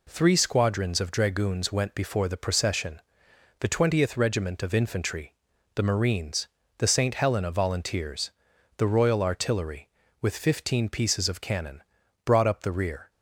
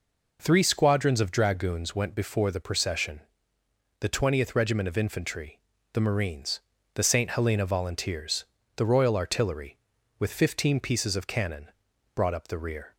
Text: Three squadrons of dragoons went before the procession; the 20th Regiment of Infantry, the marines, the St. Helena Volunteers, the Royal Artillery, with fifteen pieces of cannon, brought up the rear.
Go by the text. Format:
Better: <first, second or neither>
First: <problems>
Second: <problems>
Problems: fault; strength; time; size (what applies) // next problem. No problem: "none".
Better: neither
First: none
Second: none